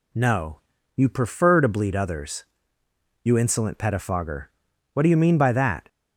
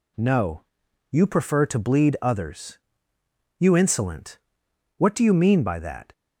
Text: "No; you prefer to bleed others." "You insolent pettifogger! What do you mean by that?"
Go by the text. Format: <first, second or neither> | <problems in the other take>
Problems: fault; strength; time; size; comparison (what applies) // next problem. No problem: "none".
first | skips "pettifogger"; at 4.6 s